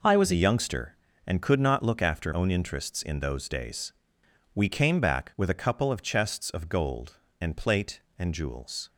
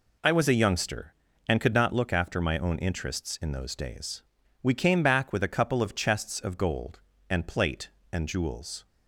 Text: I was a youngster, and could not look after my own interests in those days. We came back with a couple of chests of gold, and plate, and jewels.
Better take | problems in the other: second | skips "my"; at 2.3 s

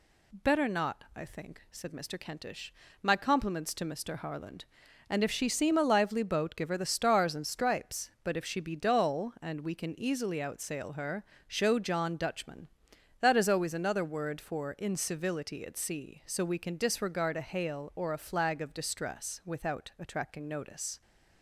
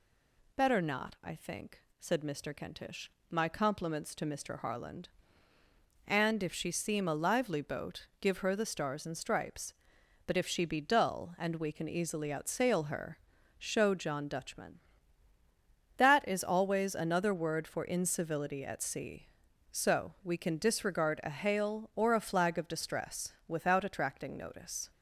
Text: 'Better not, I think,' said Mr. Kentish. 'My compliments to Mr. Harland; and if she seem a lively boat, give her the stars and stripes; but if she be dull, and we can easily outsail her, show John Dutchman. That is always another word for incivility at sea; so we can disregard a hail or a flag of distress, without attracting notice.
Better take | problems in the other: neither | none

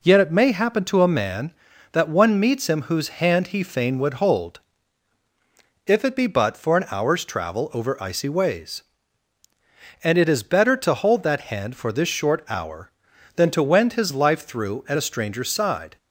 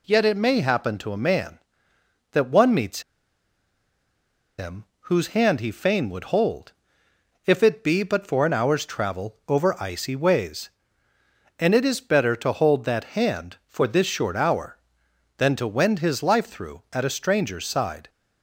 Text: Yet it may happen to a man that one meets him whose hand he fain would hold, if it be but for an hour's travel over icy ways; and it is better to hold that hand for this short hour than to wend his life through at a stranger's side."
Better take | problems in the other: first | pauses between "meets" and "him"; strong; at 3.0 s; 1.5 s long // pauses between "him" and "whose"; slight; at 4.8 s; 0.16 s long

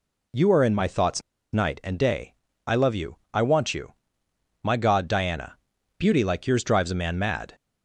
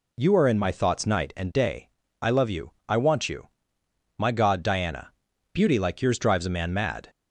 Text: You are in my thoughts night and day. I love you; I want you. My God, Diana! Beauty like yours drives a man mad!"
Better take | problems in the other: second | pauses between "thoughts" and "night"; slight; at 1.2 s; 0.32 s long

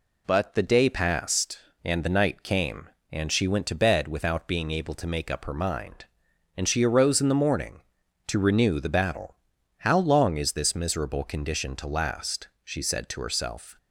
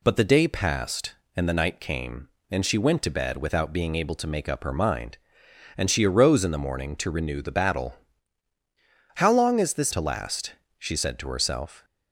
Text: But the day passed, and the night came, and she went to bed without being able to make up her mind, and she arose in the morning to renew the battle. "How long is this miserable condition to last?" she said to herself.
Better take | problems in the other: first | skips "miserable condition"; at 9.9 s

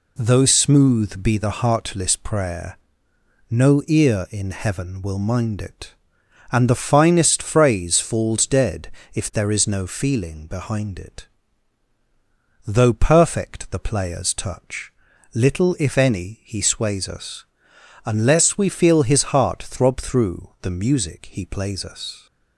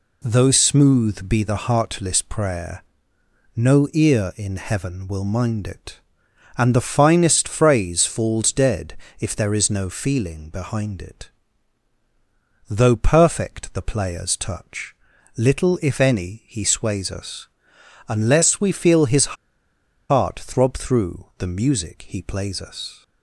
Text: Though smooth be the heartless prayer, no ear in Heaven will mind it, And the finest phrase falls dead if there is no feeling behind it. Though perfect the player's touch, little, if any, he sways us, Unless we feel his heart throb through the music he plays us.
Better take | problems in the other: first | pauses between "dead" and "if"; slight; at 8.9 s; 0.24 s long; slight in the first // pauses between "his" and "heart"; noticeable; at 19.3 s; 0.74 s long

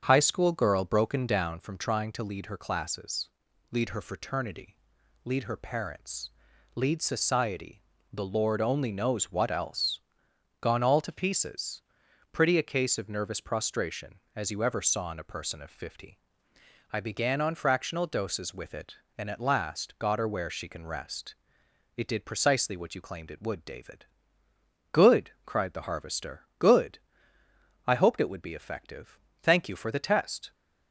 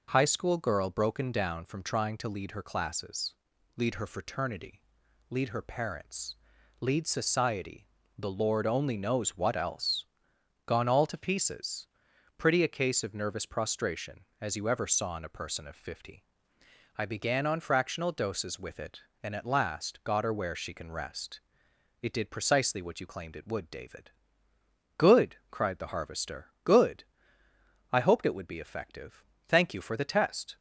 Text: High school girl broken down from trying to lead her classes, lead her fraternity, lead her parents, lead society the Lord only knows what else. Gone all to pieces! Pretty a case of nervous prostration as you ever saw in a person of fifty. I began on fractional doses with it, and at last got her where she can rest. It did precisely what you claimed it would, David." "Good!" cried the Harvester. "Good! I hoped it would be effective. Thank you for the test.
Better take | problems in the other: second | starts louder than the rest; strong; until 1.7 s; 7.5 dB // pauses between "society" and "the"; slight; at 7.7 s; 0.32 s long; slight in the second

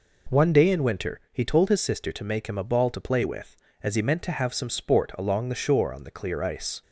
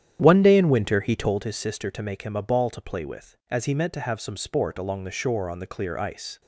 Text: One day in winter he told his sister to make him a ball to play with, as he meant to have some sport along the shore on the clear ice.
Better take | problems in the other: first | starts louder than the rest; strong; until 1.4 s; 10 dB

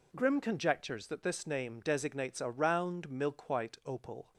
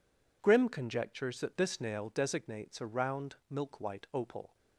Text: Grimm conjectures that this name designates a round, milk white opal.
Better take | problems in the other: first | says "nail" for "name"; at 1.7 s

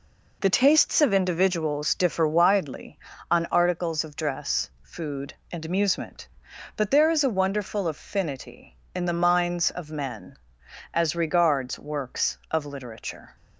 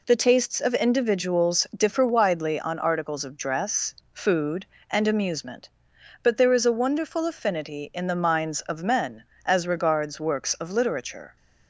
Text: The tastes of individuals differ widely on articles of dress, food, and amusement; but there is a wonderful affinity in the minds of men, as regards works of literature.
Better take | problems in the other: neither | none

